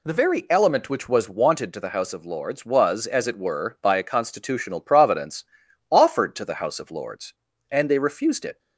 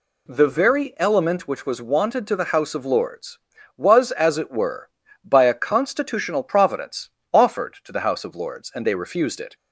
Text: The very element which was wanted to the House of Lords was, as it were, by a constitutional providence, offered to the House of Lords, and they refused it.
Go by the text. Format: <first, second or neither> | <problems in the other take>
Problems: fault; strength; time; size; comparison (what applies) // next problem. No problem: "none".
neither | none